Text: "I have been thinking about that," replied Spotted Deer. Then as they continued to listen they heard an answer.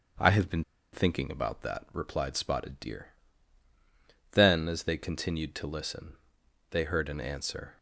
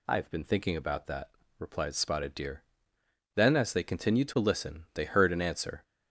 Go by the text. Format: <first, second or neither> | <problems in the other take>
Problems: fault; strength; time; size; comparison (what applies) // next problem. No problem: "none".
second | starts louder than the rest; until 1.4 s; 7 dB // pauses between "been" and "thinking"; slight; at 0.6 s; 0.30 s long // pauses between "listen" and "they"; noticeable; at 6.1 s; 0.52 s long